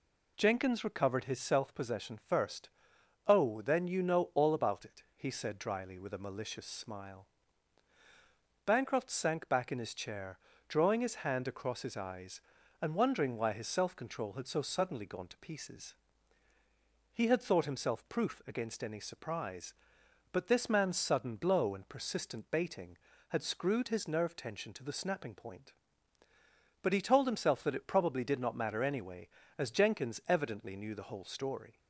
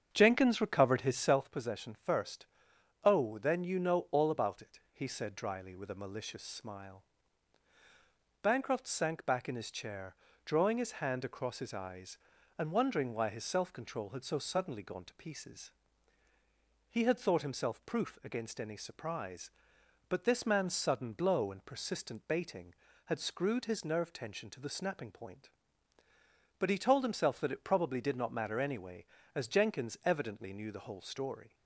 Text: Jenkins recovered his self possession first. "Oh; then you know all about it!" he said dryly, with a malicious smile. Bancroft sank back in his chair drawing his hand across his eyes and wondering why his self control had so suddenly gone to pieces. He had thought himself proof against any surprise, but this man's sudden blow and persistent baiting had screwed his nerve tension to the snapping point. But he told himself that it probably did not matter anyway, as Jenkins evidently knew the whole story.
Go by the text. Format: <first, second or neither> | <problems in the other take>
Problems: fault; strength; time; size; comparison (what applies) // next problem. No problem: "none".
first | starts louder than the rest; strong; until 1.5 s; 8 dB // pauses between "chair" and "drawing"; slight; at 10.1 s; 0.28 s long; slight in the first